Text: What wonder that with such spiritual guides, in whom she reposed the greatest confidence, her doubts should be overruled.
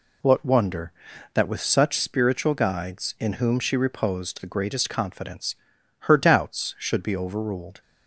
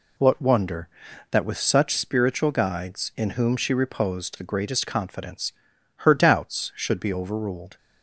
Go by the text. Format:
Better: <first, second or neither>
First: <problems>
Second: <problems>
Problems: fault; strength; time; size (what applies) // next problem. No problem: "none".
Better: neither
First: none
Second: none